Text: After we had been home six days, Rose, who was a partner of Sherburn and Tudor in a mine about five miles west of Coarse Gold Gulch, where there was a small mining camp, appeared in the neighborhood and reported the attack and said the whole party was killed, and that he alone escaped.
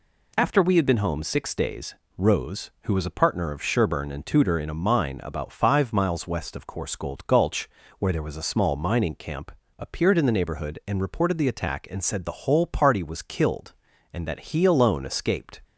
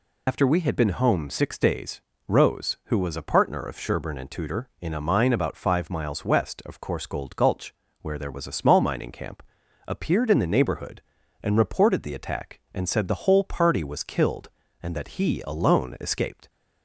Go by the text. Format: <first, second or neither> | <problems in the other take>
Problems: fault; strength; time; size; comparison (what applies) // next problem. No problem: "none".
first | loses the start of "After"; at 0.2 s; 55 ms